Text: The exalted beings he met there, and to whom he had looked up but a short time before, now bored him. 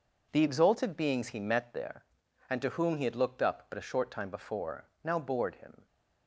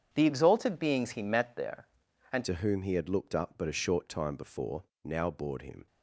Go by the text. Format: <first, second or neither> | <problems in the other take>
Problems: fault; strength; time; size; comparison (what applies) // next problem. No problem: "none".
first | starts louder than the rest; strong; until 1.1 s; 8 dB // changes voice at "to"; from 2.4 s on; 3.4 s long